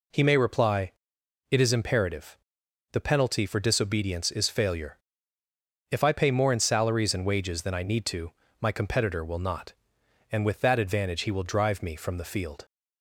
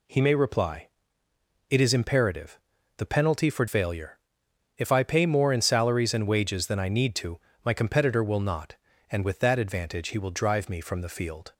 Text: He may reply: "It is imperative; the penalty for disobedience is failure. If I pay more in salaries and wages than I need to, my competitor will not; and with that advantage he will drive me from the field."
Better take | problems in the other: first | skips "disobedience is"; at 3.6 s

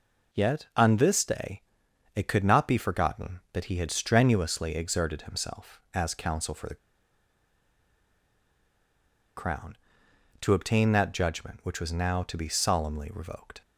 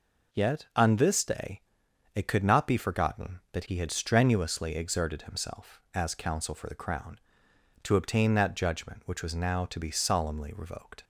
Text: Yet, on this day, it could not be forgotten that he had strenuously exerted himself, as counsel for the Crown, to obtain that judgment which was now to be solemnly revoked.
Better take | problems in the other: second | pauses between "the" and "Crown"; strong; at 6.7 s; 2.6 s long

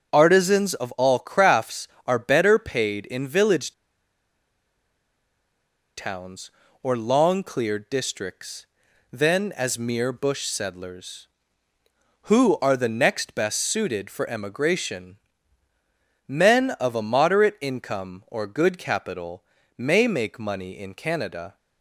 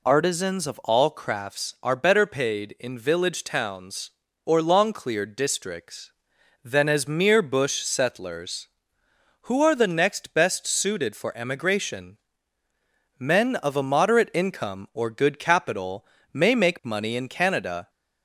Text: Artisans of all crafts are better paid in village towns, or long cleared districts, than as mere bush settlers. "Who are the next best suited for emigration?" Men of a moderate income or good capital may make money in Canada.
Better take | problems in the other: second | starts louder than the rest; until 1.1 s; 7 dB // pauses between "village" and "towns"; strong; at 3.7 s; 2.2 s long // pauses between "capital" and "may"; slight; at 19.4 s; 0.34 s long; slight in the second

